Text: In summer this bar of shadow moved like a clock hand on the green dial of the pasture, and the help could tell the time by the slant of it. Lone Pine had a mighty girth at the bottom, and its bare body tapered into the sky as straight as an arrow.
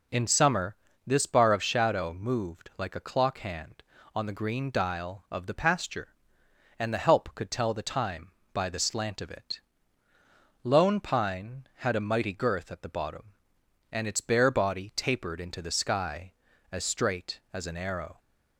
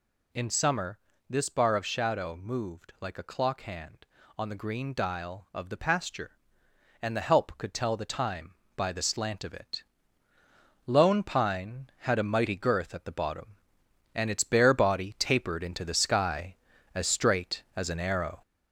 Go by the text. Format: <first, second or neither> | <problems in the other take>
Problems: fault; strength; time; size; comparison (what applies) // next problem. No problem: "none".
first | gets louder; noticeable; throughout; 4 dB // pauses between "summer" and "this"; slight; at 0.9 s; 0.32 s long; slight in the first